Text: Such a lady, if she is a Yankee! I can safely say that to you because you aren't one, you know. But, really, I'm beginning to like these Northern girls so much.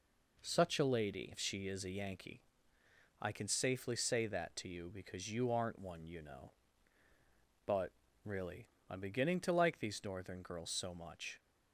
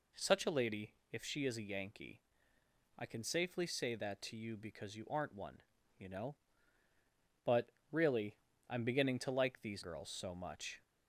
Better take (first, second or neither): first